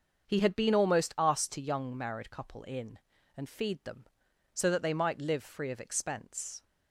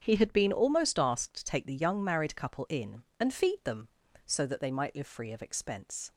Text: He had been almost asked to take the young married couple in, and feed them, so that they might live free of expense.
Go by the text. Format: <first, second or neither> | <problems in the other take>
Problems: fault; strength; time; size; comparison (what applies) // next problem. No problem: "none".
second | starts louder than the rest; until 1.3 s; 6.5 dB; strong in the second // skips "take the"; at 1.6 s